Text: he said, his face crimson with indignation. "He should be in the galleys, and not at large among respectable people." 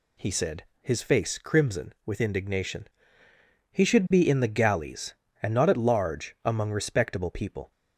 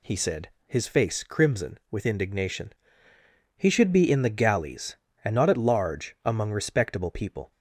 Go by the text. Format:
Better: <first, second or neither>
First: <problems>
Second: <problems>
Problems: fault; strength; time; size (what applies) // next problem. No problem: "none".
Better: neither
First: none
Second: none